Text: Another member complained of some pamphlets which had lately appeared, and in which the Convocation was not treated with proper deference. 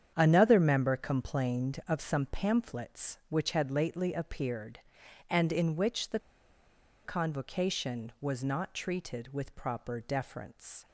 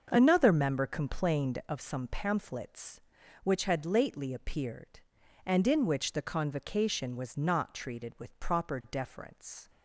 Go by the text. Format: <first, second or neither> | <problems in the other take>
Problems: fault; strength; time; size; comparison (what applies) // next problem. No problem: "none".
second | starts louder than the rest; strong; until 1.1 s; 8.5 dB; also in the second // pauses between "the" and "Convocation"; noticeable; at 6.1 s; 0.85 s long